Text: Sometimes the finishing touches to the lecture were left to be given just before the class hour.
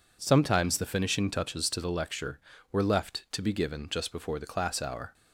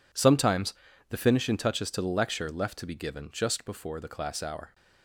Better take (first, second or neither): first